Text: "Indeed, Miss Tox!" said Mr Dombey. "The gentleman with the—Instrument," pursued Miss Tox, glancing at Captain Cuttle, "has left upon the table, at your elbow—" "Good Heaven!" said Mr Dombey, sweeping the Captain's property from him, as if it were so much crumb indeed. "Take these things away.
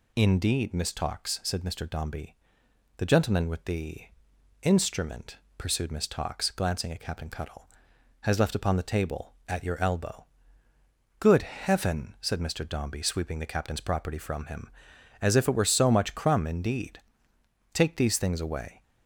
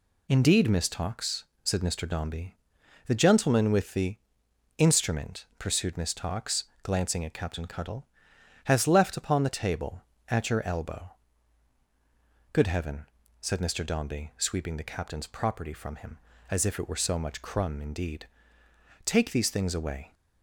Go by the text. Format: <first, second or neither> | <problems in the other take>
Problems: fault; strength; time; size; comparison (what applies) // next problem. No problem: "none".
neither | none